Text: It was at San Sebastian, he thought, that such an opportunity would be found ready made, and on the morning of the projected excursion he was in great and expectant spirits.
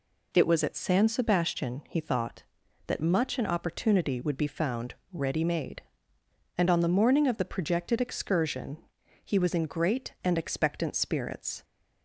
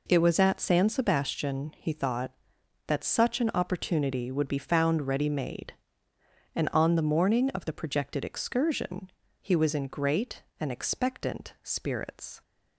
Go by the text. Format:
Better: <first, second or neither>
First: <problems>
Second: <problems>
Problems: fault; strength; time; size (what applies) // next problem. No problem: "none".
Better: second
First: says "much" for "such"; at 2.9 s // pauses between "found" and "ready"; slight; at 4.9 s; 0.18 s long // pauses between "excursion" and "he"; noticeable; at 8.7 s; 0.46 s long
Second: pauses between "excursion" and "he"; slight; at 9.1 s; 0.30 s long